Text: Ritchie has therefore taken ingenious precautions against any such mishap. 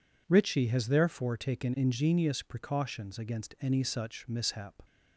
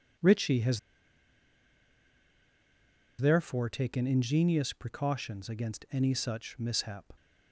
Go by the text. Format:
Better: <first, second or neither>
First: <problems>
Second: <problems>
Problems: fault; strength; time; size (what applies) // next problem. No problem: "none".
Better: first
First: none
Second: pauses between "has" and "therefore"; strong; at 0.7 s; 2.4 s long